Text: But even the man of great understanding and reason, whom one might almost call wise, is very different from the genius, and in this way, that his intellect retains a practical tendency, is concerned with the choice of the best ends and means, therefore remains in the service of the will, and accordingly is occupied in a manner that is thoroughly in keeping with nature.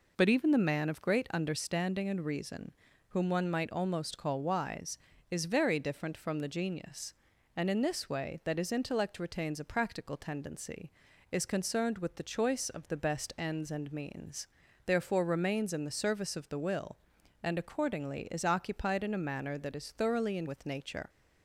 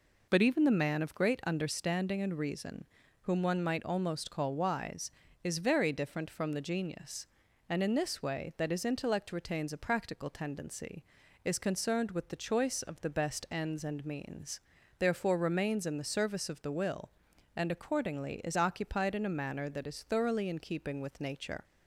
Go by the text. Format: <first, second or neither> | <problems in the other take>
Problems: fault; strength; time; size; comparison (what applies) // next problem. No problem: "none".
second | skips "keeping"; at 20.4 s